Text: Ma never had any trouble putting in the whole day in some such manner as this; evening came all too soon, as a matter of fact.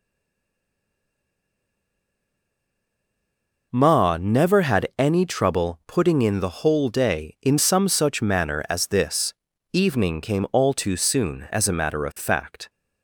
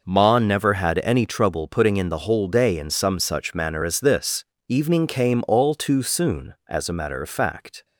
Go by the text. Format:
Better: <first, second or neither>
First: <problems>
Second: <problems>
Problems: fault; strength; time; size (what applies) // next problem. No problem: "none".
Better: second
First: stays silent before the first word; strong; until 3.7 s; 3.7 s long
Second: none